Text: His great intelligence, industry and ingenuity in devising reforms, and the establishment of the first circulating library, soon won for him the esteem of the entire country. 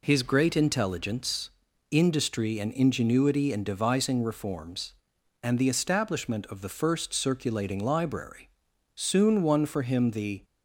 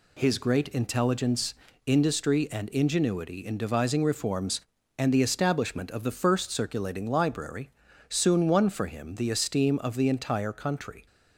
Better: second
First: stops before "esteem of the entire country"; at 10.4 s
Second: none

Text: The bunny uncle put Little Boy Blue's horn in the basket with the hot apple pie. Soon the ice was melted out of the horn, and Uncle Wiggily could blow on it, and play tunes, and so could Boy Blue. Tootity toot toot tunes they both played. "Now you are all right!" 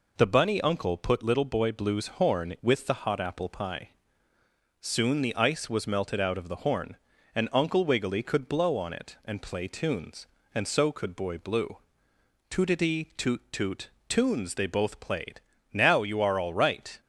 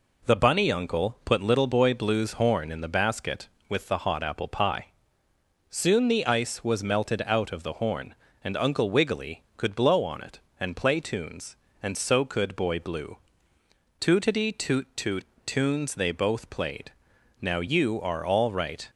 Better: second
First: skips "in the basket"; at 2.5 s // pauses between "toot" and "tunes"; slight; at 13.8 s; 0.20 s long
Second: pauses between "toot" and "tunes"; slight; at 15.2 s; 0.20 s long

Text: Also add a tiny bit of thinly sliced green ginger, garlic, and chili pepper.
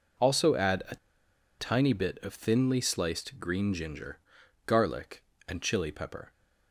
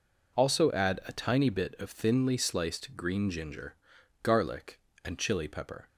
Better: second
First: pauses between "a" and "tiny"; noticeable; at 0.9 s; 0.63 s long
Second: none

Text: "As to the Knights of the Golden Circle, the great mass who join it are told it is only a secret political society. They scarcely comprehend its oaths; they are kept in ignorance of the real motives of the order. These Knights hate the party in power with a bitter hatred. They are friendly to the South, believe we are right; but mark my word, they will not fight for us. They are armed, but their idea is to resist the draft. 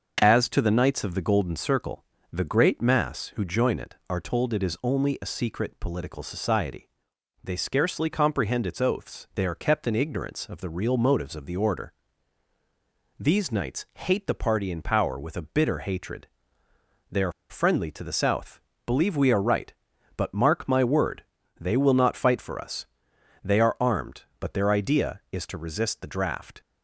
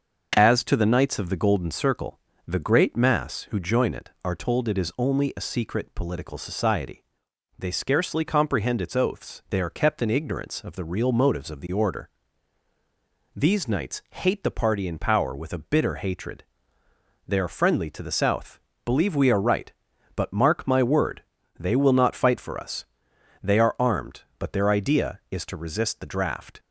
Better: second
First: starts louder than the rest; until 1.2 s; 6.5 dB // pauses between "are" and "friendly"; slight; at 17.3 s; 0.18 s long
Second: starts louder than the rest; until 1.3 s; 6.5 dB

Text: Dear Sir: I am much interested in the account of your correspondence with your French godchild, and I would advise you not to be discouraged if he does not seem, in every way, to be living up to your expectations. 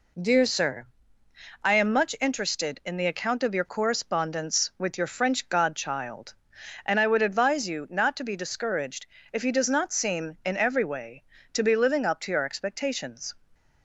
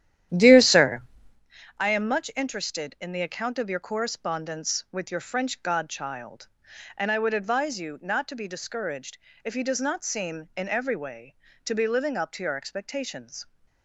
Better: first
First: pauses between "discouraged" and "if"; slight; at 9.0 s; 0.24 s long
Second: starts louder than the rest; strong; until 1.4 s; 11.5 dB // pauses between "discouraged" and "if"; slight; at 9.1 s; 0.24 s long

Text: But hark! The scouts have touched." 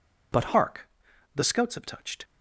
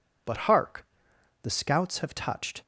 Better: second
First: changes voice at "hark"; from 0.5 s on; 1.7 s long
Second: none

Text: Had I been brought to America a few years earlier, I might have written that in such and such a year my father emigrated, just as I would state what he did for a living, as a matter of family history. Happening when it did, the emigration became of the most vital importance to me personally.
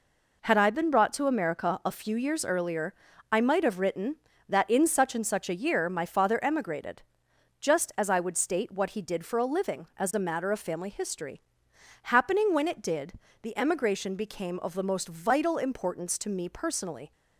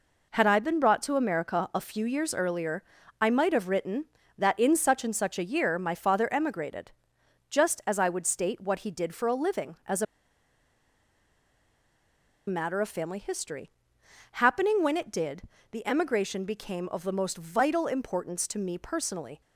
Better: first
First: none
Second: pauses between "a" and "matter"; strong; at 10.0 s; 2.4 s long

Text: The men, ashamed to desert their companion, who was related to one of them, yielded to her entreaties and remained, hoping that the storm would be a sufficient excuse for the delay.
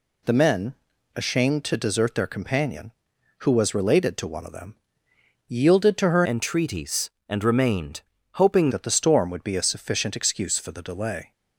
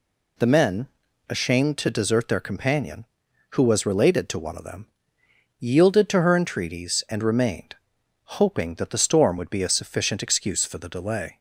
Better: second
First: changes voice from "entreaties" to "hoping"; from 6.2 to 8.7 s; 2.5 s long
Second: none

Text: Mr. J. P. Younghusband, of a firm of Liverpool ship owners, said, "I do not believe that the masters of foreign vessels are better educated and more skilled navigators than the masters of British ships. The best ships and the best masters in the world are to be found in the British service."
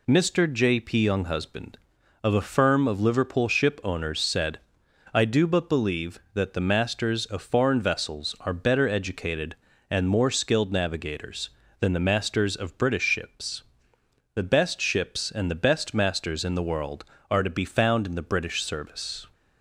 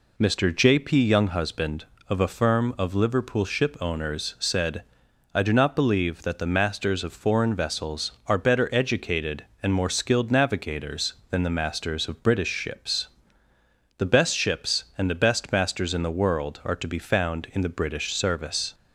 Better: second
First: says "but" for "not"; at 5.4 s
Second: none

